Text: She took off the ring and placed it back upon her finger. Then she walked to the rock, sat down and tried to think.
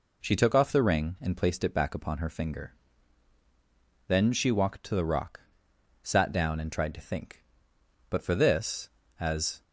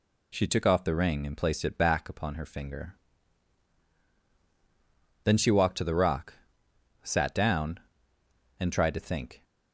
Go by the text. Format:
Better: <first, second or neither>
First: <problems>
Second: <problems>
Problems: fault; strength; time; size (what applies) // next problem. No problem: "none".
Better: second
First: goes on to say "But for this as"; from 8.0 s on; 1.5 s long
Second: none